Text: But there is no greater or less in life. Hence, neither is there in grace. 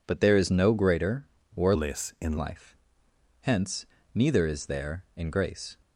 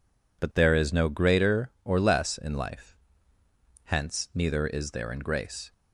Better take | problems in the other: second | changes voice from "less" to "in"; from 1.7 to 2.3 s; 0.6 s long

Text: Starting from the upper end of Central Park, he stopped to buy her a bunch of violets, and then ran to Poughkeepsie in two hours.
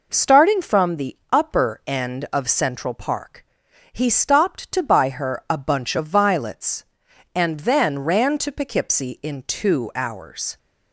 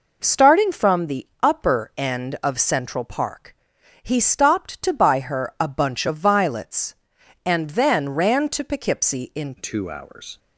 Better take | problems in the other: first | pauses between "the" and "upper"; slight; at 1.2 s; 0.16 s long; slight in the first // changes voice at "two"; from 9.5 s on; 0.8 s long

